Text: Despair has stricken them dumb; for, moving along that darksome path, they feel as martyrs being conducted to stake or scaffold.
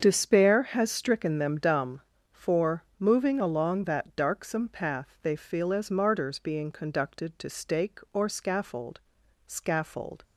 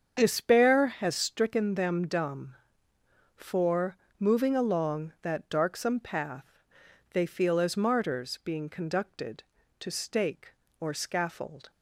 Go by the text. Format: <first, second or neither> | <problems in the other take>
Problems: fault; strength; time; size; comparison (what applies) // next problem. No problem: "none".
second | starts louder than the rest; until 1.0 s; 7 dB; strong in the second // says "scaffold" twice; at 9.4 s